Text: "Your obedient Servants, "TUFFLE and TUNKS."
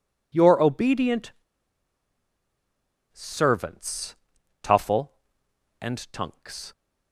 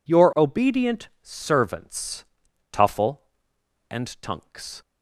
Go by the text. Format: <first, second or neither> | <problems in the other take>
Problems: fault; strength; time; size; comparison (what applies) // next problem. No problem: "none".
second | pauses between "obedient" and "Servants"; strong; at 1.3 s; 1.7 s long